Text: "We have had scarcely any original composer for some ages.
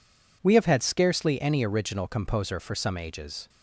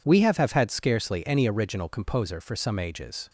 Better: first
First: none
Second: says "have" twice; at 0.3 s

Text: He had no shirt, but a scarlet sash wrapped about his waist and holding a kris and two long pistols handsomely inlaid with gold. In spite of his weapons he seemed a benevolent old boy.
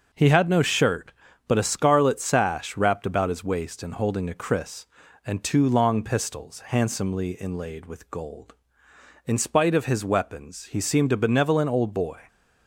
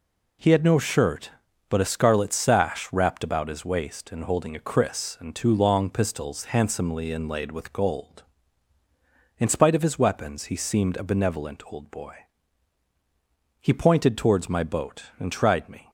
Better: first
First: none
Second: goes on to say "He pointed towards my boat and tried me"; strong; from 13.5 s on; 2.3 s long

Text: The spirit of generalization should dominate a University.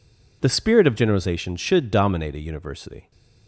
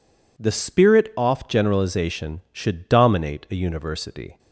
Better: first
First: none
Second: says "off" for "of"; at 1.1 s

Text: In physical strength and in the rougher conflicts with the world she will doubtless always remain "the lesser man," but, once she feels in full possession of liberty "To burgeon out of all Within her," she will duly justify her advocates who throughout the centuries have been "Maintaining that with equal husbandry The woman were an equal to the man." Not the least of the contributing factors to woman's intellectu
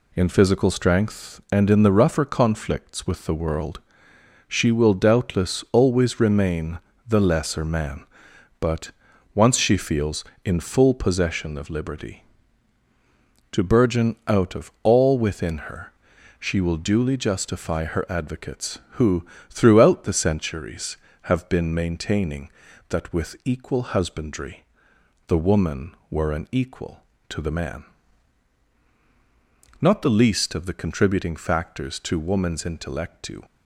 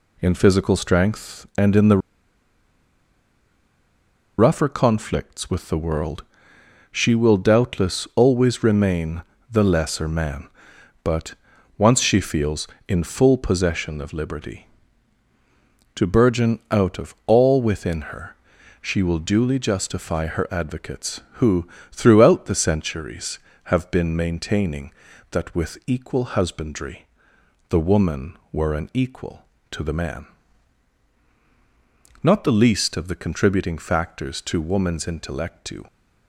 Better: first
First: pauses between "world" and "she"; noticeable; at 3.8 s; 0.66 s long // pauses between "remain" and "the"; slight; at 6.7 s; 0.30 s long // pauses between "who" and "throughout"; slight; at 19.2 s; 0.24 s long // pauses between "husbandry" and "The"; noticeable; at 24.6 s; 0.64 s long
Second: pauses between "the" and "rougher"; strong; at 1.9 s; 2.4 s long // pauses between "world" and "she"; noticeable; at 6.2 s; 0.66 s long // pauses between "remain" and "the"; slight; at 9.2 s; 0.30 s long // pauses between "who" and "throughout"; slight; at 21.6 s; 0.24 s long // pauses between "husbandry" and "The"; noticeable; at 27.0 s; 0.64 s long

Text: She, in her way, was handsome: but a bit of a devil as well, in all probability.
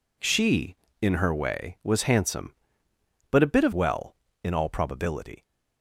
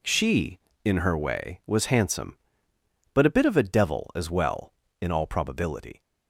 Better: second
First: skips "a devil as"; at 3.7 s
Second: none

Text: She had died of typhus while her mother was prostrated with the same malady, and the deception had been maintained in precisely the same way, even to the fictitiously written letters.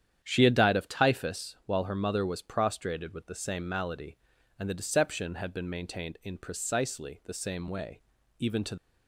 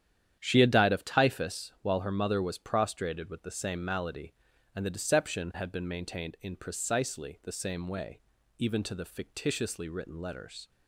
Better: second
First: starts louder than the rest; strong; until 1.2 s; 9.5 dB // stops before "the fictitiously written letters"; at 8.7 s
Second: starts louder than the rest; strong; until 1.4 s; 10 dB

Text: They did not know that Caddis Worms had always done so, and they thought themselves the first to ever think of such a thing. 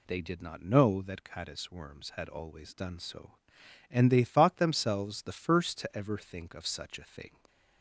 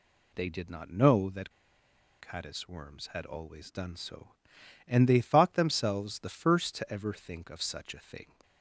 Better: first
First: none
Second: pauses between "that" and "Caddis"; noticeable; at 1.5 s; 0.69 s long

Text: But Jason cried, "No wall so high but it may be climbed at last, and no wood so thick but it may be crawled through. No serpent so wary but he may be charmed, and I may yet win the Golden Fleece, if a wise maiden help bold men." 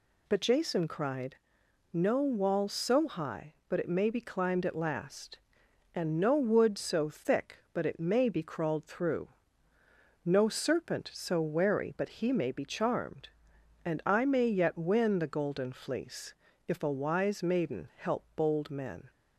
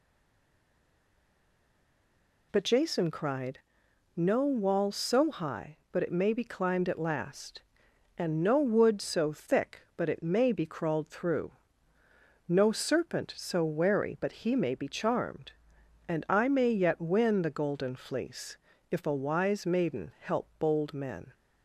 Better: first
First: none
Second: stays silent before the first word; until 2.5 s; 2.5 s long

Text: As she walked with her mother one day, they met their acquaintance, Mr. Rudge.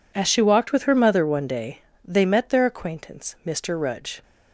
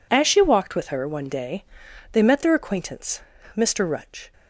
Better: first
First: none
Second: skips "mother"; at 1.0 s

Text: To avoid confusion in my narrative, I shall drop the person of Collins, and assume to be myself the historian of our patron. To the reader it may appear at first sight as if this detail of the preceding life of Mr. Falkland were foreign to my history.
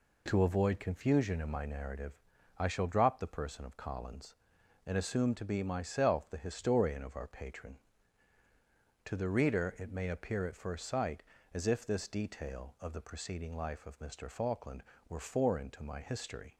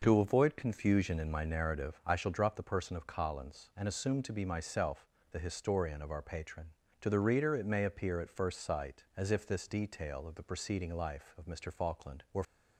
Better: first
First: none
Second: pauses between "myself" and "the"; slight; at 5.0 s; 0.24 s long // stops before "foreign to my history"; at 12.4 s

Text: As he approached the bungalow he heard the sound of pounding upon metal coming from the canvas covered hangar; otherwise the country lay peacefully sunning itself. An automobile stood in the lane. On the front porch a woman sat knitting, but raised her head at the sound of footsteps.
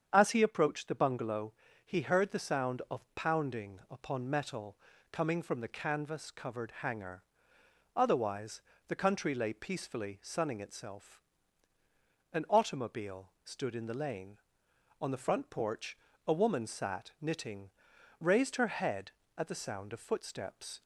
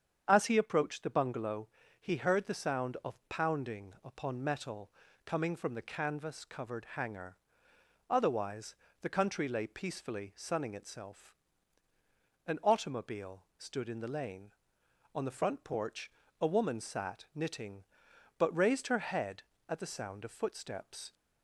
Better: second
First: starts louder than the rest; strong; until 1.1 s; 8 dB // pauses between "bungalow" and "he"; slight; at 1.5 s; 0.32 s long // pauses between "metal" and "coming"; slight; at 4.7 s; 0.34 s long // pauses between "otherwise" and "the"; slight; at 8.6 s; 0.26 s long // pauses between "porch" and "a"; slight; at 15.9 s; 0.28 s long // skips "but"; at 17.9 s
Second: starts louder than the rest; strong; until 1.2 s; 8 dB // pauses between "bungalow" and "he"; slight; at 1.6 s; 0.32 s long // pauses between "metal" and "coming"; slight; at 4.9 s; 0.34 s long // pauses between "otherwise" and "the"; slight; at 8.7 s; 0.26 s long // pauses between "porch" and "a"; slight; at 16.1 s; 0.28 s long

